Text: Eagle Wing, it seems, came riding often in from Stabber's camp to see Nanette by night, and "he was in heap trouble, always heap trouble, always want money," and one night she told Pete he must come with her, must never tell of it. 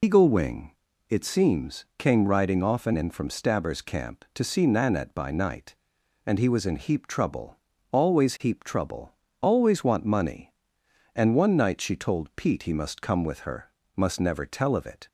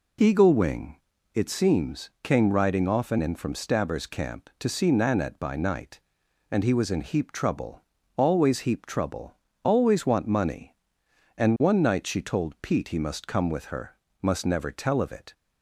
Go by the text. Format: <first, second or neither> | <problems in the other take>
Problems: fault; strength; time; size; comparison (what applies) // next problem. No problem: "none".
second | loses the start of "Eagle"; at 0.0 s; 95 ms